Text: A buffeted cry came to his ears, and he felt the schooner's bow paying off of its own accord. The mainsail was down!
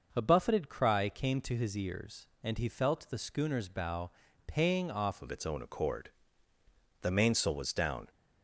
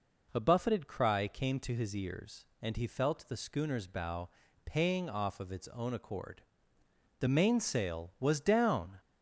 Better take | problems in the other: second | pauses between "bow" and "paying"; slight; at 4.1 s; 0.34 s long; slight in the second // changes voice at "of"; from 5.2 s on; 2.8 s long

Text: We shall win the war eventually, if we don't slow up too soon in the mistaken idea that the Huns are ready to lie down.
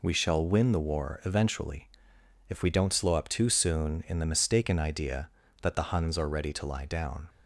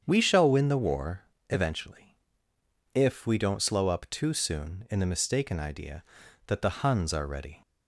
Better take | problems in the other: first | starts louder than the rest; strong; until 1.0 s; 8 dB // pauses between "war" and "eventually"; slight; at 1.2 s; 0.26 s long // stops before "to lie down"; at 7.6 s

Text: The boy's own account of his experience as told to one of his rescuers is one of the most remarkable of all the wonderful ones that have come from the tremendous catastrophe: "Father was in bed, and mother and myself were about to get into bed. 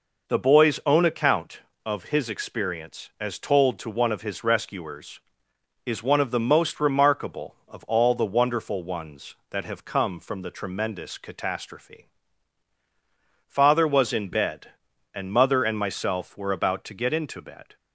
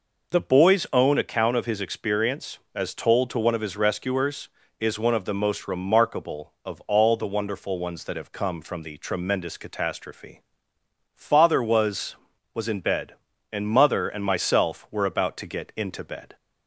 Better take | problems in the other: first | says "was" twice; at 12.5 s

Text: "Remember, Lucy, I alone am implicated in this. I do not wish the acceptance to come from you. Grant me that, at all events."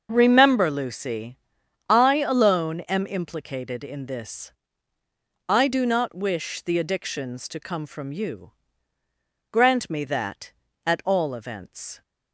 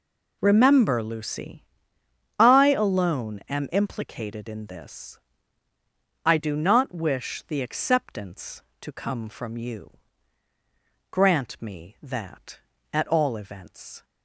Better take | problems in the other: second | starts louder than the rest; until 1.1 s; 6.5 dB // says "addictions" for "acceptance"; at 6.7 s

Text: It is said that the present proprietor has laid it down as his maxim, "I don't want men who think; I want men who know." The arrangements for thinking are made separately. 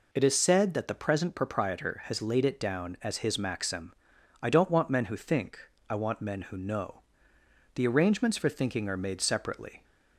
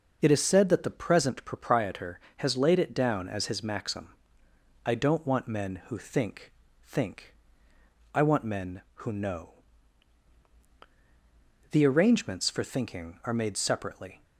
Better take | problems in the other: first | says "think" twice; at 6.8 s

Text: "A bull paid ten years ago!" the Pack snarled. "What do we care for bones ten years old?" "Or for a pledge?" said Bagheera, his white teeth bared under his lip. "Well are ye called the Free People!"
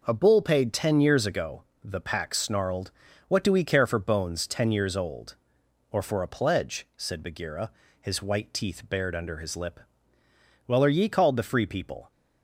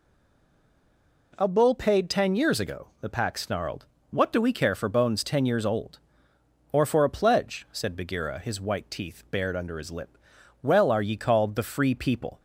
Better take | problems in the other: first | stays silent before the first word; noticeable; until 1.3 s; 1.3 s long

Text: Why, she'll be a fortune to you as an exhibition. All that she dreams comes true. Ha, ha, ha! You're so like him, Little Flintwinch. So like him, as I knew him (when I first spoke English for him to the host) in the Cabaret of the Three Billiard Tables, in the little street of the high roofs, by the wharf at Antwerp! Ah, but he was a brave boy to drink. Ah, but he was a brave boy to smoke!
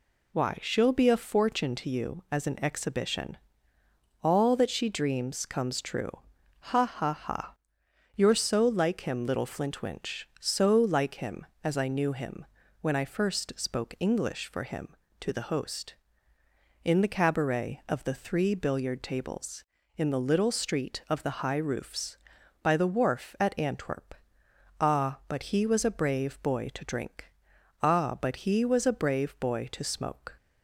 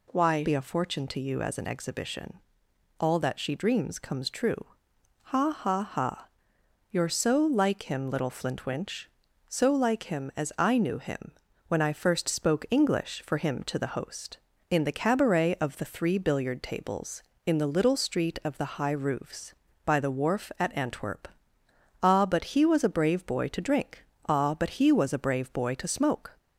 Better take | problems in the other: first | skips "she'll"; at 0.4 s

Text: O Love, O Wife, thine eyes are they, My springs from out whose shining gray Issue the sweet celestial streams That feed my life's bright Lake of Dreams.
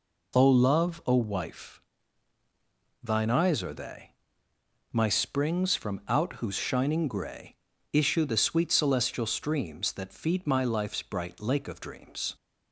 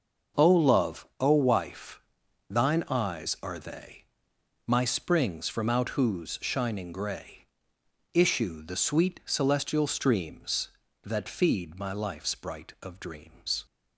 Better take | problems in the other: first | starts louder than the rest; noticeable; until 1.4 s; 6 dB // pauses between "gray" and "Issue"; noticeable; at 7.4 s; 0.68 s long; also in the first // skips "Lake"; at 12.7 s

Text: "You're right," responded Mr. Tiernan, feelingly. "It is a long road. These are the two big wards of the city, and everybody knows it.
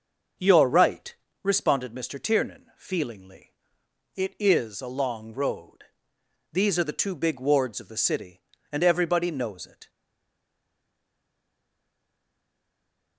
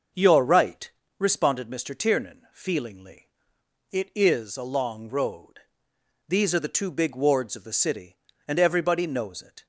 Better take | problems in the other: second | stays silent after the last word; strong; from 9.8 s on; 3.3 s long

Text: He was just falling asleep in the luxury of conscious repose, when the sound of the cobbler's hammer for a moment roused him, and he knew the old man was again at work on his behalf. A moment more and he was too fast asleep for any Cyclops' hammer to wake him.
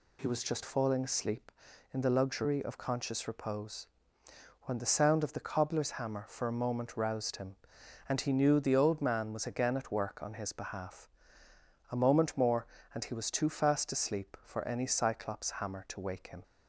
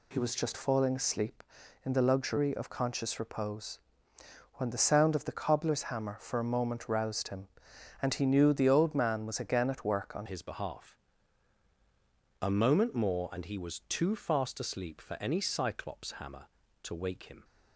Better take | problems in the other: first | changes voice at "his"; from 10.2 s on; 7.2 s long

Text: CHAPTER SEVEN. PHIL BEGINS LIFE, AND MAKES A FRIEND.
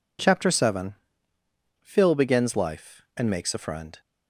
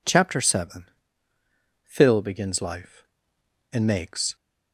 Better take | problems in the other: first | stops before "A FRIEND"; at 4.3 s

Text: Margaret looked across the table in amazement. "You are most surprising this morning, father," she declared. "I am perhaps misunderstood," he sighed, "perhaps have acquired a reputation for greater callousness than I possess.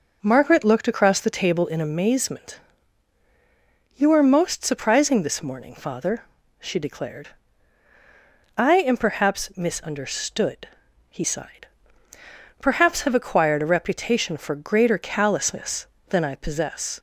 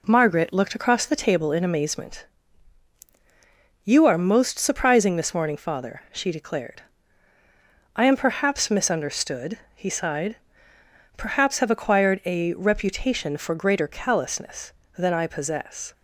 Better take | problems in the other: neither | none

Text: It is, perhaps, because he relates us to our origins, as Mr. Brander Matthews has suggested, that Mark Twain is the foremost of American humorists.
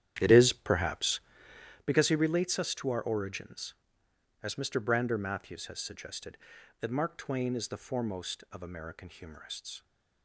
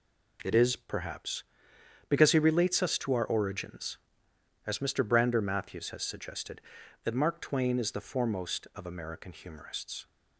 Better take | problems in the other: second | starts louder than the rest; strong; until 1.9 s; 10.5 dB

